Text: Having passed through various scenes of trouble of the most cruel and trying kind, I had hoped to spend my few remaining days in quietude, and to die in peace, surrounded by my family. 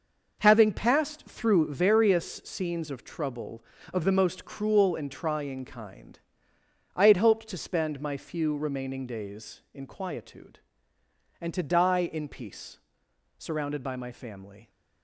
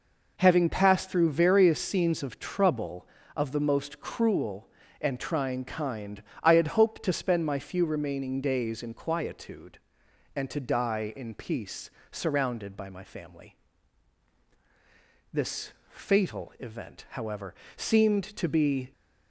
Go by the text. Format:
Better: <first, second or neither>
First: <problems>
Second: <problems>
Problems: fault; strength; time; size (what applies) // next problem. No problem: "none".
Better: first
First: none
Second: goes on to say "This fatal event however seemed to be"; strong; from 15.3 s on; 3.5 s long